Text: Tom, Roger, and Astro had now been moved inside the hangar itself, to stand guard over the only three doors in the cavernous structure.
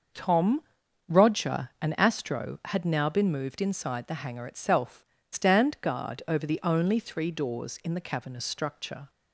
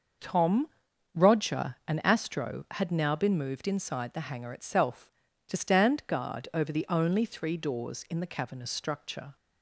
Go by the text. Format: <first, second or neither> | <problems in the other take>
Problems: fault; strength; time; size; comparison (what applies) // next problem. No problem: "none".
second | starts louder than the rest; noticeable; until 1.6 s; 6 dB; noticeable in the second // skips "to"; at 5.1 s